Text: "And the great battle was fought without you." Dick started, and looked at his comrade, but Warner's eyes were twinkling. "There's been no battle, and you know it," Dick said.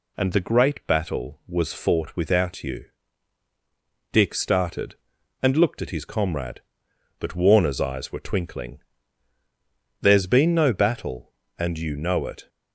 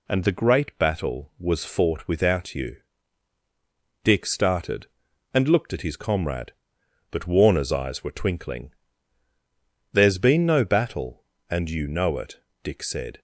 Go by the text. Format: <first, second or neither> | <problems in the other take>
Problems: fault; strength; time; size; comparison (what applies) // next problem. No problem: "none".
second | stops before "Dick said"; at 12.4 s